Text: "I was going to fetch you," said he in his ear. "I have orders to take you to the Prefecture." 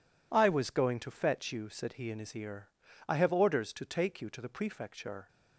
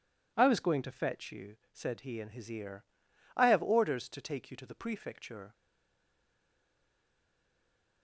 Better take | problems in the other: first | stays silent after the last word; from 5.5 s on; 2.5 s long

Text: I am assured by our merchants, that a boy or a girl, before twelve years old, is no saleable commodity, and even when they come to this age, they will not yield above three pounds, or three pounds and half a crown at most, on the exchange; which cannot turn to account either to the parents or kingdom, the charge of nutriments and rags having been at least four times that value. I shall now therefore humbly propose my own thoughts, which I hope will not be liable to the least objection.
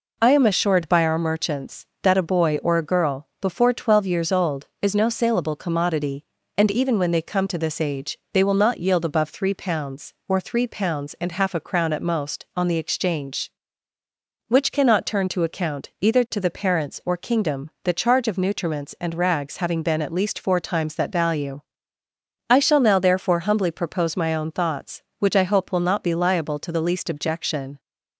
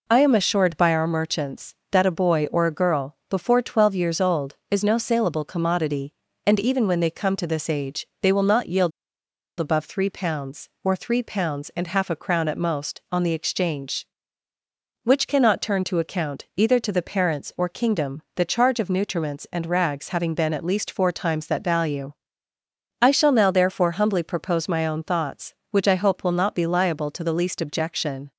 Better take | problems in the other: first | pauses between "yield" and "above"; noticeable; at 8.9 s; 0.68 s long

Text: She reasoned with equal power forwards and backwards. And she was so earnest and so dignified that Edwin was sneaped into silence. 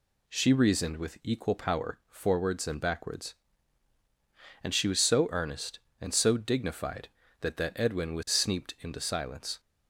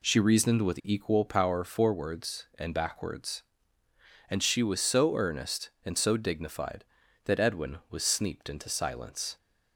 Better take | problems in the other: second | says "that" twice; at 7.5 s

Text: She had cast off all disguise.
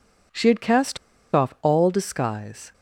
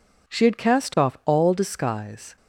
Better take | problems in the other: second | pauses between "cast" and "off"; at 0.9 s; 0.37 s long

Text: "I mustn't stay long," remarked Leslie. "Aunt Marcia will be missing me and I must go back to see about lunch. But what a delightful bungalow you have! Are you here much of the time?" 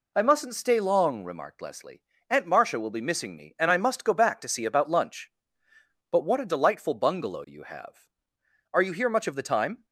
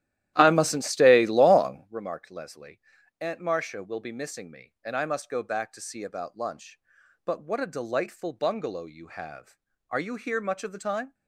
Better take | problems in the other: first | starts louder than the rest; strong; until 1.9 s; 13 dB

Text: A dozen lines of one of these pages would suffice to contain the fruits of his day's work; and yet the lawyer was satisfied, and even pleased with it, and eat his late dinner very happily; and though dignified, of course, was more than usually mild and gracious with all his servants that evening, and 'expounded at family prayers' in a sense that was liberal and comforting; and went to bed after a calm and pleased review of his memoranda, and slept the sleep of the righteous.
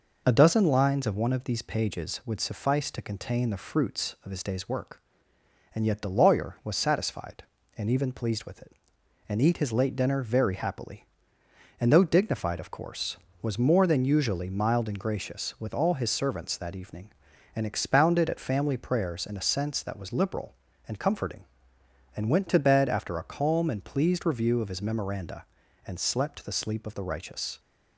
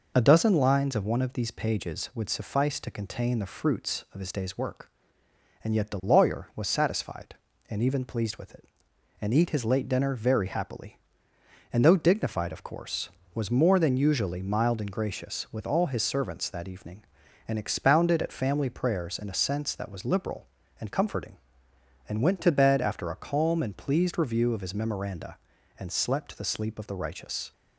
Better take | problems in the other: neither | none

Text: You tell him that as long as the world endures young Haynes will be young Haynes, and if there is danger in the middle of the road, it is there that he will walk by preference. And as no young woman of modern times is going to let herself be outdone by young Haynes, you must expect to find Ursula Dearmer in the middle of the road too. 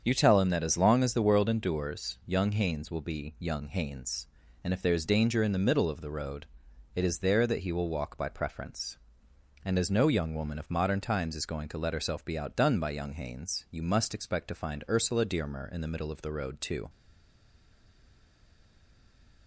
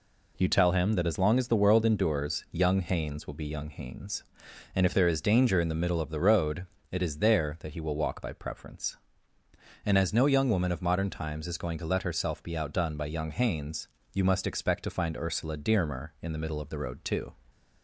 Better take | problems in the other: second | starts louder than the rest; strong; until 1.0 s; 7.5 dB // stays silent after the last word; strong; from 16.8 s on; 2.6 s long

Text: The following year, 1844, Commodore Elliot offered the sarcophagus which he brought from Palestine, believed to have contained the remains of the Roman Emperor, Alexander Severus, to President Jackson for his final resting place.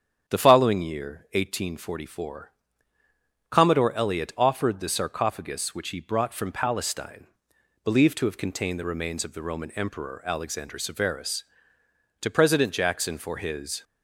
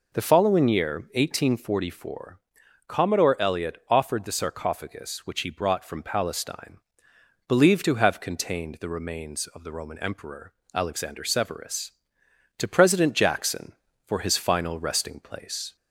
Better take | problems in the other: second | starts louder than the rest; strong; until 1.3 s; 7.5 dB // stops before "final resting place"; at 13.8 s

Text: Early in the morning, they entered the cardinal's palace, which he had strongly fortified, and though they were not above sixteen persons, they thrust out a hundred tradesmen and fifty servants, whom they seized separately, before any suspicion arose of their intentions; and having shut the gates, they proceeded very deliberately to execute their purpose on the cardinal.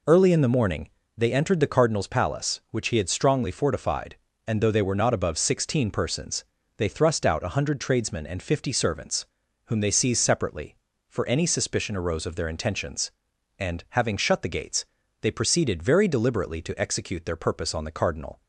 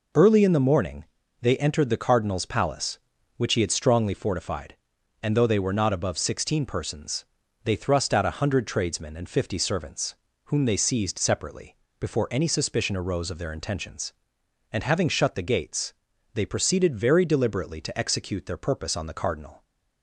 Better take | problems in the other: second | says "for" for "before"; at 11.0 s

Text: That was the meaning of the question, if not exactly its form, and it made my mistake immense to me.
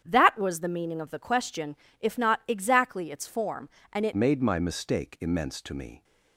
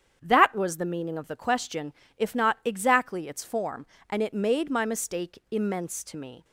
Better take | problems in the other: second | starts louder than the rest; strong; until 1.0 s; 8.5 dB; strong in the second // changes voice at "made"; from 4.1 s on; 1.9 s long

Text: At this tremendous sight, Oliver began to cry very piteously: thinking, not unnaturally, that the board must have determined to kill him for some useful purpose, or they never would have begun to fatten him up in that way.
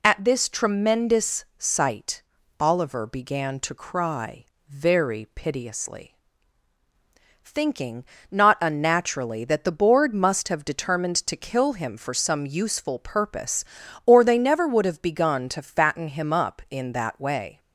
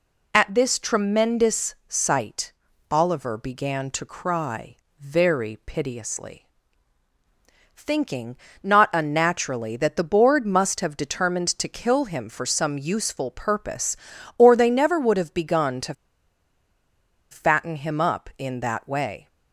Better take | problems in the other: first | pauses between "cry" and "very"; slight; at 4.7 s; 0.20 s long; slight in the first // pauses between "to" and "fatten"; strong; at 15.9 s; 1.3 s long

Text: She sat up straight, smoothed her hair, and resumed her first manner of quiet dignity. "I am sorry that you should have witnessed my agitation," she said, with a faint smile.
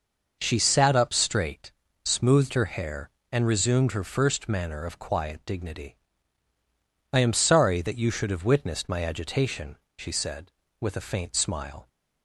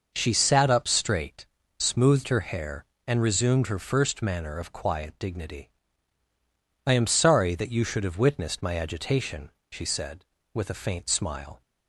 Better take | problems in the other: neither | none

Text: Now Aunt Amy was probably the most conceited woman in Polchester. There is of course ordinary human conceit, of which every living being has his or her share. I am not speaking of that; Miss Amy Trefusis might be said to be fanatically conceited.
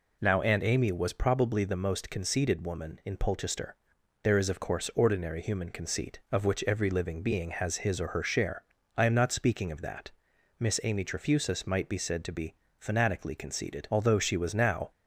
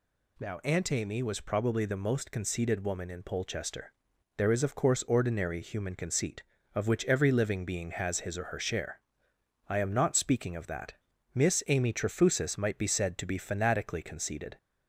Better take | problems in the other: second | pauses between "be" and "fanatically"; slight; at 12.5 s; 0.24 s long // goes on to say "Although she was now"; noticeable; from 13.9 s on; 1.0 s long

